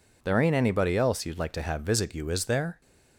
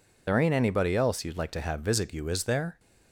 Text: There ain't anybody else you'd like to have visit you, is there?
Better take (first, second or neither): first